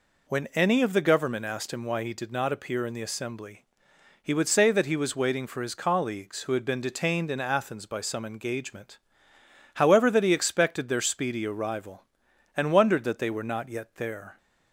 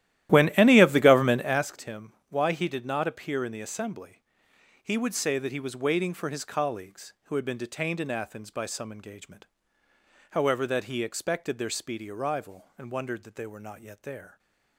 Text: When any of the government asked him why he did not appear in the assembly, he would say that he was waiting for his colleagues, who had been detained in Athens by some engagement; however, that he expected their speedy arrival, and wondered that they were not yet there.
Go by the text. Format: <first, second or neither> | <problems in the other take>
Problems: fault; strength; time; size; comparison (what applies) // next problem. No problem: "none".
first | starts louder than the rest; strong; until 1.7 s; 13.5 dB // pauses between "him" and "why"; slight; at 2.1 s; 0.16 s long